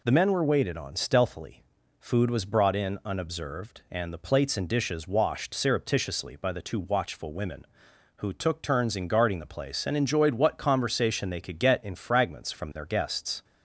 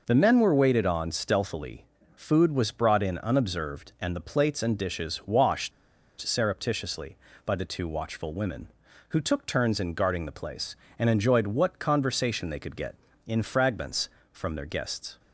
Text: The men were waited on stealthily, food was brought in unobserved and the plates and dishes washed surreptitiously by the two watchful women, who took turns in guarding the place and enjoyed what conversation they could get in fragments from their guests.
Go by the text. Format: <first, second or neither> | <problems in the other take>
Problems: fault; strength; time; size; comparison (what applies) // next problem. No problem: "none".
first | pauses between "washed" and "surreptitiously"; noticeable; at 5.7 s; 0.49 s long